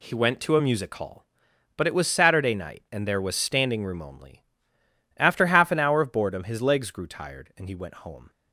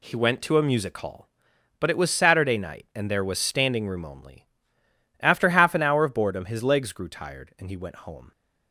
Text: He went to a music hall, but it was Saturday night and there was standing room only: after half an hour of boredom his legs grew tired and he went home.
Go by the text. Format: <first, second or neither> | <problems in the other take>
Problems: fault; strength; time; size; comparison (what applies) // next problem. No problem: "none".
neither | none